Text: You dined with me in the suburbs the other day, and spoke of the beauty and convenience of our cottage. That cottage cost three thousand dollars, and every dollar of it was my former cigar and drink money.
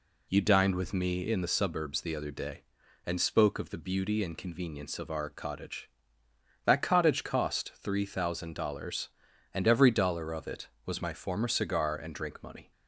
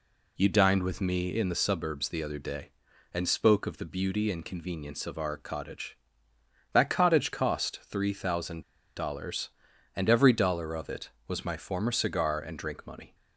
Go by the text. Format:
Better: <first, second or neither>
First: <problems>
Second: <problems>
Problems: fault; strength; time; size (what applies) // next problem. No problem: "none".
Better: first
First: none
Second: pauses between "thousand" and "dollars"; slight; at 8.6 s; 0.34 s long